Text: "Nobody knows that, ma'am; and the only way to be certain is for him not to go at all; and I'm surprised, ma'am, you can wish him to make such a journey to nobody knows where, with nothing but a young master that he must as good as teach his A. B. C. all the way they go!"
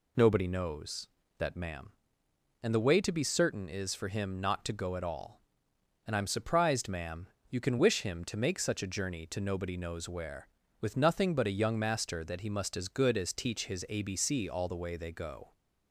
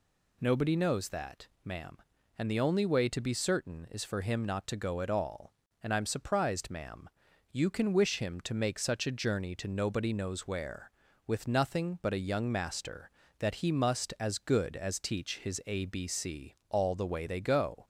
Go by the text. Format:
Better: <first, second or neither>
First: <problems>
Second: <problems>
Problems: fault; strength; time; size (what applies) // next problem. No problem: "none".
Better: second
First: skips "only"; at 2.8 s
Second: none